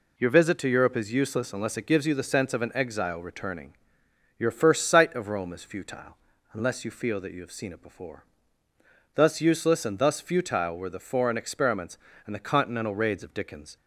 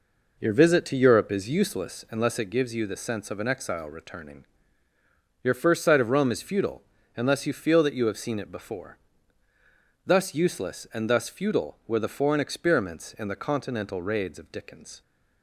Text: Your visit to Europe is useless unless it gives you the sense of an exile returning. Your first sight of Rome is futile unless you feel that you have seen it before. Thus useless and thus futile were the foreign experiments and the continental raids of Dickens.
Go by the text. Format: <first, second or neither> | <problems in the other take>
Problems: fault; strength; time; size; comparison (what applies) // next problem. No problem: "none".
first | starts louder than the rest; noticeable; until 1.9 s; 4.5 dB // pauses between "futile" and "unless"; slight; at 6.8 s; 0.32 s long; also in the first